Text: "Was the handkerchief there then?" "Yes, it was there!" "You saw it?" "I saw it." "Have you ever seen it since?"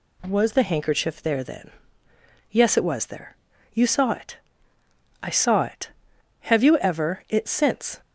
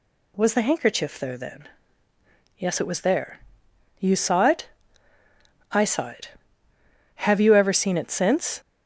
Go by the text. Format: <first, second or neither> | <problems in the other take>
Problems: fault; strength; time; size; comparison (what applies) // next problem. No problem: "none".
second | skips "seen"; at 7.2 s